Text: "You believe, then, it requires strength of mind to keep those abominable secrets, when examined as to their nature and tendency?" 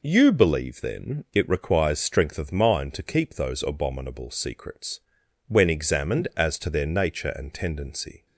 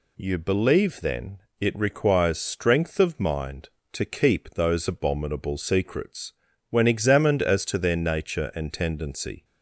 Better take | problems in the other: neither | none

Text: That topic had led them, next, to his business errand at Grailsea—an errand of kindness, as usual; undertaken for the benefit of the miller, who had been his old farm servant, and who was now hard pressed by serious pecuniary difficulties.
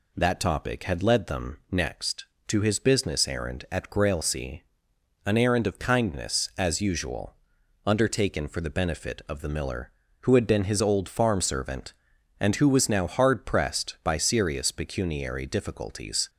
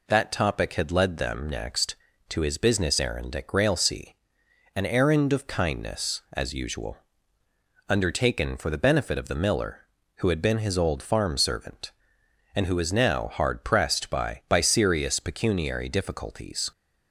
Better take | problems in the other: first | says "by" twice; at 14.4 s

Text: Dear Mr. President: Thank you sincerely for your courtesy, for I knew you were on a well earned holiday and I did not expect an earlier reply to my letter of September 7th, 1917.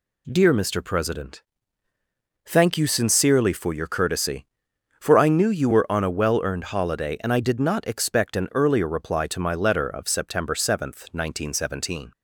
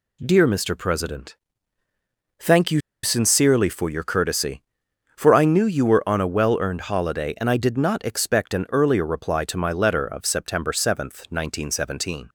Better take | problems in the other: first | pauses between "you" and "sincerely"; slight; at 2.8 s; 0.22 s long

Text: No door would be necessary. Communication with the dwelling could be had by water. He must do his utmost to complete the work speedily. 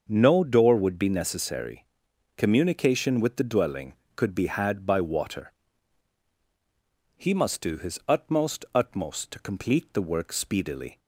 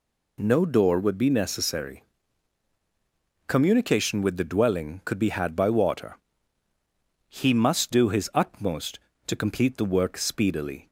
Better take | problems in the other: second | starts louder than the rest; until 1.0 s; 6.5 dB // says "utmost" twice; at 8.7 s

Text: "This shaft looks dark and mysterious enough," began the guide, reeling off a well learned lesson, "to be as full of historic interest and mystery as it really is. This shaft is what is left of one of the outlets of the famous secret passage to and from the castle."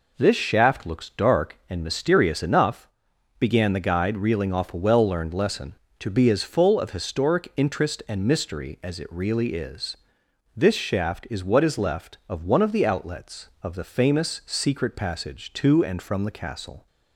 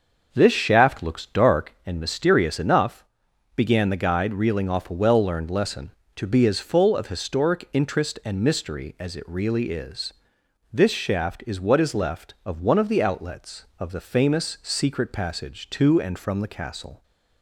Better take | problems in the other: first | starts louder than the rest; until 1.8 s; 6 dB

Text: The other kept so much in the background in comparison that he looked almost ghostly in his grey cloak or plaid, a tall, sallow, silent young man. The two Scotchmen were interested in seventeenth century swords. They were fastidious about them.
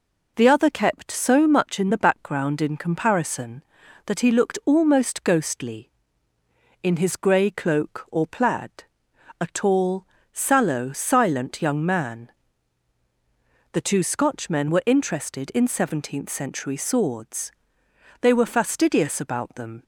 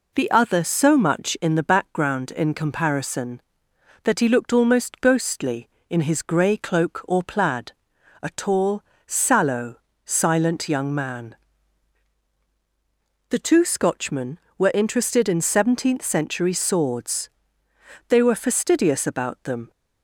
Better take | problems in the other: first | skips "kept"; at 0.6 s

